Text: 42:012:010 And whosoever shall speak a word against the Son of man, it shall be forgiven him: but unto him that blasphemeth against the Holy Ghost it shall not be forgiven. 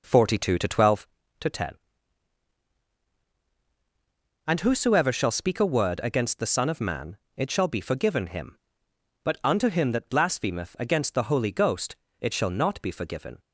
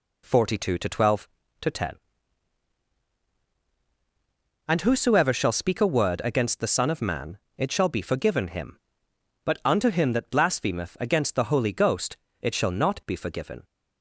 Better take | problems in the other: second | starts louder than the rest; noticeable; until 1.1 s; 5 dB // pauses between "Ghost" and "it"; slight; at 11.9 s; 0.24 s long; slight in the second

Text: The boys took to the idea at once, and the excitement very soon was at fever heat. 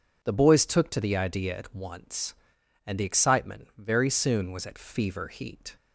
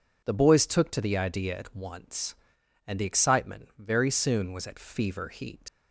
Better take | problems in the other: first | leaves "heat" unfinished; at 5.6 s; 80 ms

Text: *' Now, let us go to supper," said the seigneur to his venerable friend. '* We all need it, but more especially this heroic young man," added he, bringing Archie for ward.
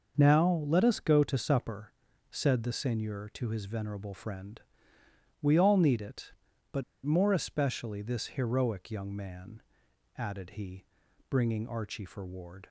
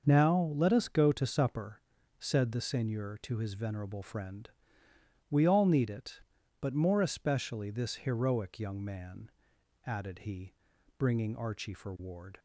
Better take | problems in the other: second | starts louder than the rest; noticeable; until 1.1 s; 6 dB; also in the second // pauses between "but" and "more"; slight; at 6.8 s; 0.22 s long

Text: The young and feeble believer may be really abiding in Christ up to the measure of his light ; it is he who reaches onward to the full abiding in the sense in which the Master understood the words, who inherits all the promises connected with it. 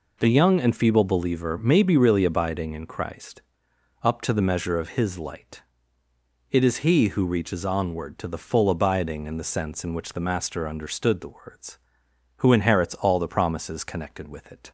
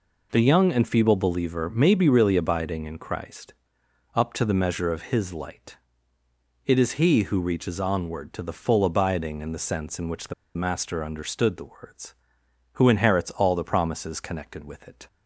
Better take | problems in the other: first | pauses between "Christ" and "up"; noticeable; at 3.5 s; 0.60 s long; noticeable in the first // pauses between "the" and "Master"; slight; at 10.3 s; 0.23 s long

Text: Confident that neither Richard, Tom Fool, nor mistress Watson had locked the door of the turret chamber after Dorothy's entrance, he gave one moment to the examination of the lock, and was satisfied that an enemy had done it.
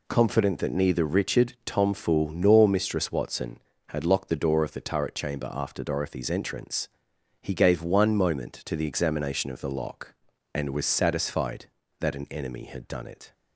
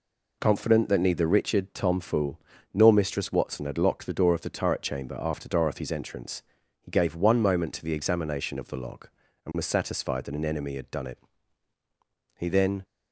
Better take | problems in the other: first | goes on to say "He then"; slight; from 12.3 s on; 0.46 s long

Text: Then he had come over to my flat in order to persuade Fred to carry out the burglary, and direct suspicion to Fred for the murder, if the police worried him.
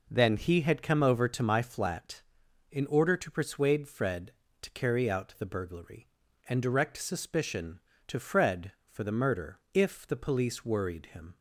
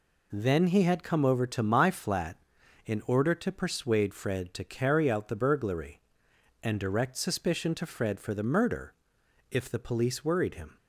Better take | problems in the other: neither | none

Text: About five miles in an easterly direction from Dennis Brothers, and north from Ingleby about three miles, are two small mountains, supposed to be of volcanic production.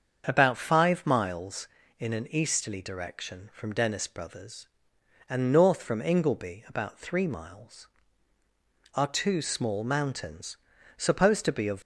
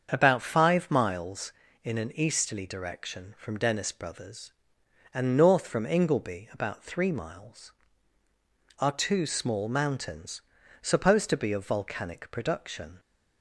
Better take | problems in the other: second | starts louder than the rest; strong; until 1.2 s; 7 dB; strong in the second // stops before "volcanic production"; at 11.8 s

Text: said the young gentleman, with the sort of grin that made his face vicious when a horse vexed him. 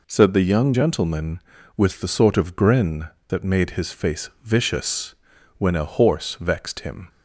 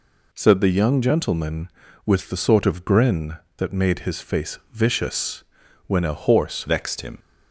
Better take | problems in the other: first | pauses between "vicious" and "when"; at 5.4 s; 0.44 s long; also in the first // changes voice at "vexed"; from 6.6 s on; 0.5 s long

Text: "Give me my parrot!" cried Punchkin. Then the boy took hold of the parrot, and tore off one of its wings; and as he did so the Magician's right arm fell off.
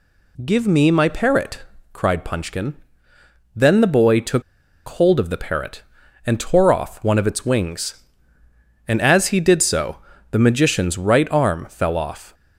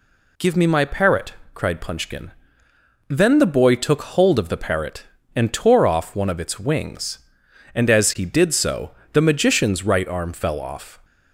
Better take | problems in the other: second | pauses between "took" and "hold"; noticeable; at 4.4 s; 0.47 s long // pauses between "so" and "the"; slight; at 9.9 s; 0.34 s long; slight in the second

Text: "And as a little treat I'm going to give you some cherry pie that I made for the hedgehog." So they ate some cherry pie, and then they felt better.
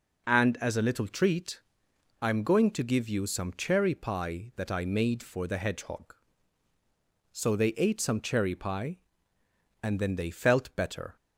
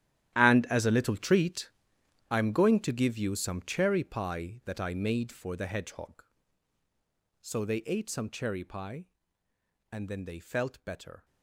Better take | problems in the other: first | gets quieter; strong; throughout; 17 dB // pauses between "treat" and "I'm"; noticeable; at 1.6 s; 0.60 s long; noticeable in the first

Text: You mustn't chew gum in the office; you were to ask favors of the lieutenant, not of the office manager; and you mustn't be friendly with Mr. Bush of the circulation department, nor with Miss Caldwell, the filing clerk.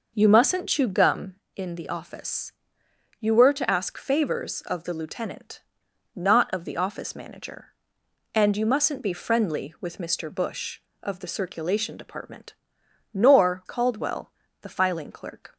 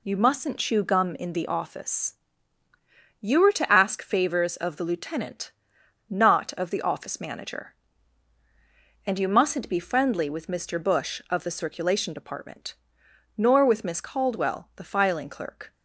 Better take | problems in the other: second | skips "with Miss"; at 13.6 s

